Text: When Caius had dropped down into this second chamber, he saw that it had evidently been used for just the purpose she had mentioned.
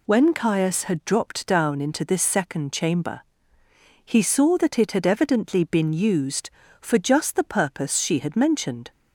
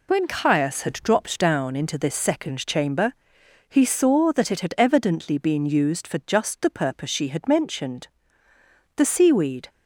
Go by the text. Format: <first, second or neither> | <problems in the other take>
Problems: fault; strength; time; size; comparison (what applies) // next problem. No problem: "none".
first | goes on to say "The seaweed"; noticeable; from 8.9 s on; 0.74 s long